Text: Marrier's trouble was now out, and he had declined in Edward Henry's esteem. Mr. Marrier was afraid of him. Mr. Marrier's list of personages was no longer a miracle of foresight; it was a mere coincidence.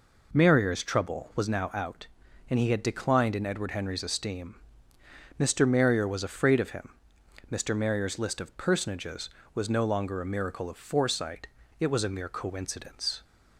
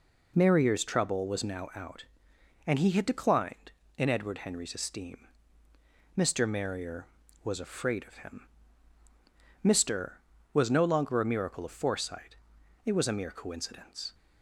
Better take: first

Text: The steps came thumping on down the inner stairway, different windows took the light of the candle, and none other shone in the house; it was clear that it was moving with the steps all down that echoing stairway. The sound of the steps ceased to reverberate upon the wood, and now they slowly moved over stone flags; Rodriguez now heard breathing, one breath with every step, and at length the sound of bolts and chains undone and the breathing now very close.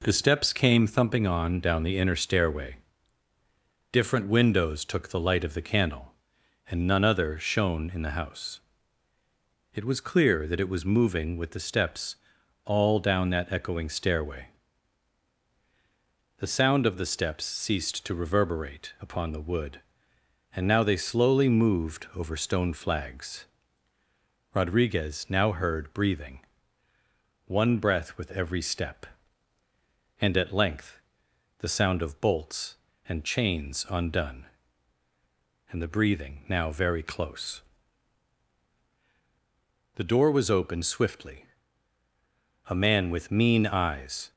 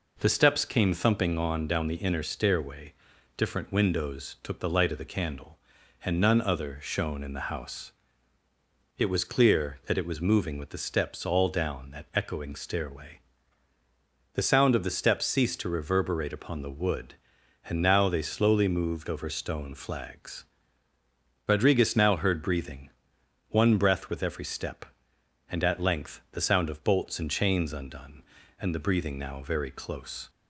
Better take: second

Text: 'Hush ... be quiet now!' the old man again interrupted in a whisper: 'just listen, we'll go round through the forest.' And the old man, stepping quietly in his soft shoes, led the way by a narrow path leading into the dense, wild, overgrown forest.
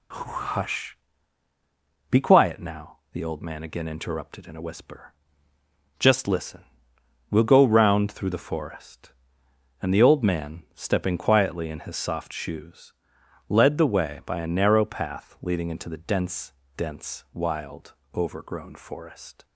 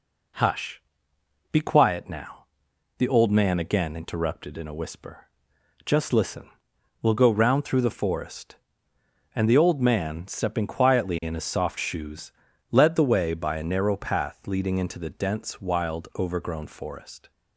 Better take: second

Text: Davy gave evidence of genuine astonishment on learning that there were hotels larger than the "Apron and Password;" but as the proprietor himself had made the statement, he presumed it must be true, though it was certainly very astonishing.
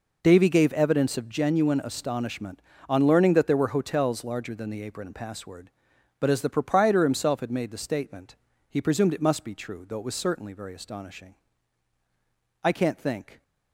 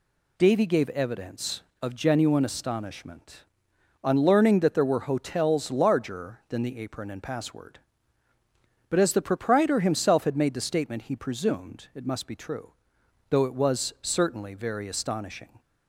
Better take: second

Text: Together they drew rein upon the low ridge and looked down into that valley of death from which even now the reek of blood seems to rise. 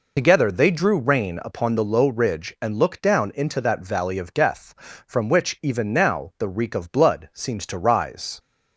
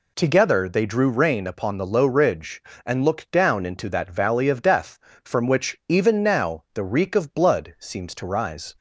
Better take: second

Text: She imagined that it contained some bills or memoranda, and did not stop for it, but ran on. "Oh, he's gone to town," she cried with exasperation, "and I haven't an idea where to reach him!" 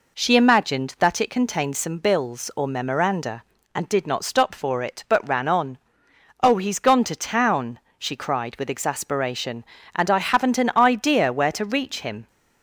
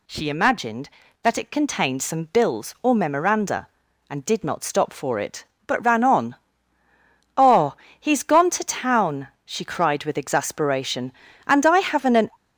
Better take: first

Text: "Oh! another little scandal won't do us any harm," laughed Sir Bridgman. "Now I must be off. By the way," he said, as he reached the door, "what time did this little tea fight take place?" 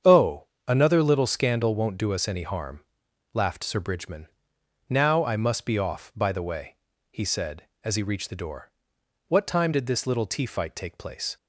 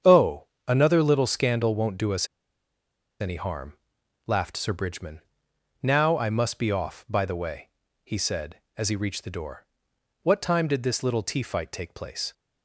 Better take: first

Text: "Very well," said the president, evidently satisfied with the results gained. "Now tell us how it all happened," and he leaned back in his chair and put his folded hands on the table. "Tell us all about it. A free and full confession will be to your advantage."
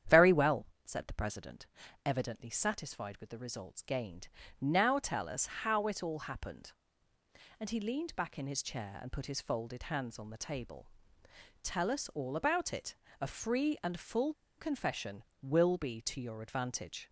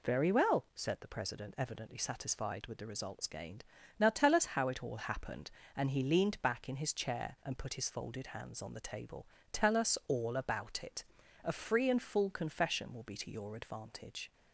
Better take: second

